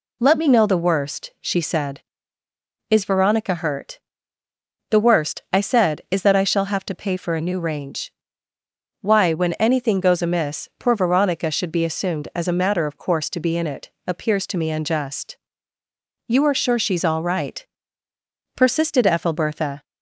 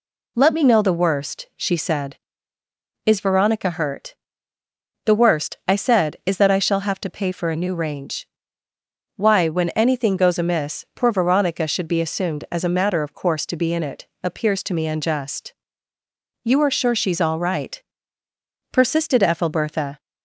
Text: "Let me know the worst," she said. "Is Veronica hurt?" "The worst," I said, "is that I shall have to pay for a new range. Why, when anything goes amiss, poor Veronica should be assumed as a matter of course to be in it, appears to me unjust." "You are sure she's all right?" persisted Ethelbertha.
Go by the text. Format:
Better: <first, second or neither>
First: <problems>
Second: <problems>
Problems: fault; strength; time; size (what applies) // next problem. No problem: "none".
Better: neither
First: none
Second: none